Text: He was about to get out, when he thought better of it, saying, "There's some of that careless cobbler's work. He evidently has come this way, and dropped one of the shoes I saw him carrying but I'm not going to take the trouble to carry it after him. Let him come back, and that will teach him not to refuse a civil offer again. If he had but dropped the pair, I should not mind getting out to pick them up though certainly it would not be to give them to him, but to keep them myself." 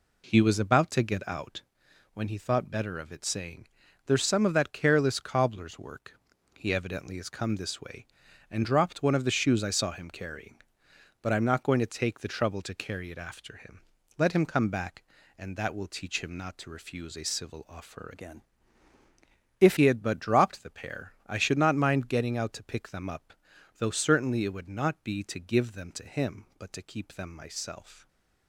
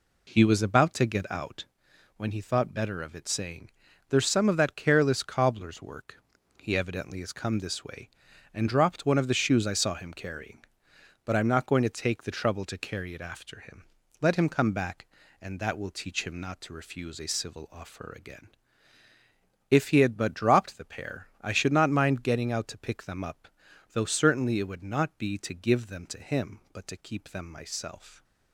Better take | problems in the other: second | changes voice from "again" to "If"; from 18.1 to 19.7 s; 1.6 s long // pauses between "up" and "though"; at 23.3 s; 0.44 s long; also in the second // stays silent after the last word; slight; from 27.9 s on; 0.5 s long

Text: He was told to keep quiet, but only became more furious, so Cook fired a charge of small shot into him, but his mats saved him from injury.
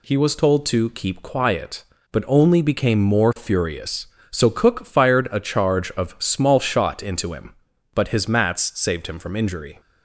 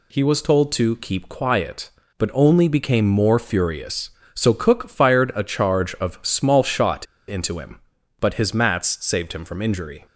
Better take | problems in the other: first | pauses between "shot" and "into"; slight; at 7.0 s; 0.22 s long

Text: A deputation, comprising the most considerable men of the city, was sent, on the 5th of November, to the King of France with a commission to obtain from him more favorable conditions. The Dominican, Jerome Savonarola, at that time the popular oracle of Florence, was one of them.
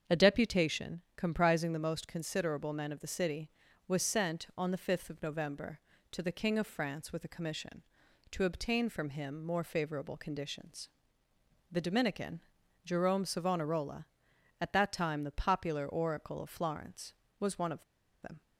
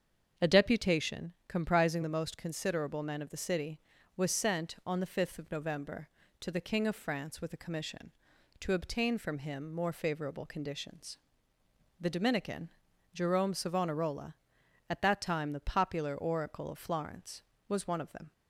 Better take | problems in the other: second | starts louder than the rest; strong; until 1.2 s; 7.5 dB; strong in the second // pauses between "of" and "them"; at 17.8 s; 0.41 s long

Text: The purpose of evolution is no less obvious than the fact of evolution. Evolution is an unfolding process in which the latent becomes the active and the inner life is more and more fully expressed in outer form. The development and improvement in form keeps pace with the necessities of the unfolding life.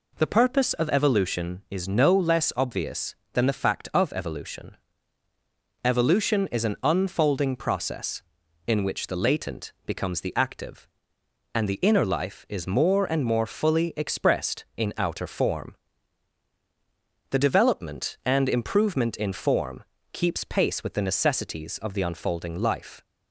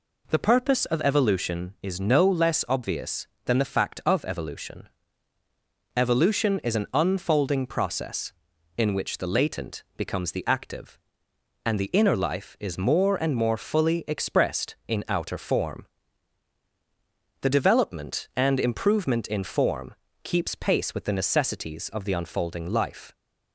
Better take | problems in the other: neither | pauses between "latent" and "becomes"; slight; the same in both // pauses between "form" and "keeps"; slight; the same in both

